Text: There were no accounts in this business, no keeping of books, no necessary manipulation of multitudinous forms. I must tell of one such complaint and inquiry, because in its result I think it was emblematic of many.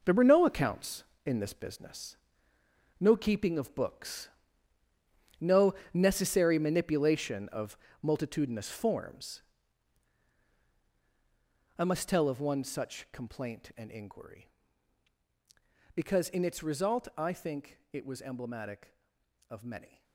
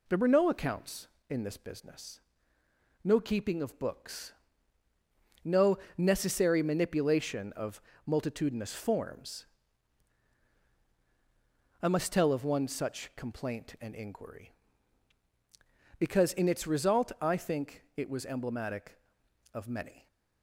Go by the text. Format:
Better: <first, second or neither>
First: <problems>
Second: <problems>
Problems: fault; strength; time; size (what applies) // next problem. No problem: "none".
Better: second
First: gets quieter; strong; throughout; 10 dB // pauses between "no" and "necessary"; slight; at 5.7 s; 0.20 s long // pauses between "of" and "multitudinous"; slight; at 7.7 s; 0.24 s long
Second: pauses between "no" and "necessary"; slight; at 5.7 s; 0.20 s long // pauses between "of" and "multitudinous"; slight; at 7.8 s; 0.24 s long